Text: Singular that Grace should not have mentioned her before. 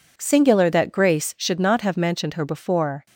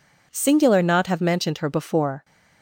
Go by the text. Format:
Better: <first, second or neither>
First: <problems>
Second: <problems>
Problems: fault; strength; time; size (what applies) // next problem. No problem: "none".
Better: first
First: none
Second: skips "that Grace should"; at 0.8 s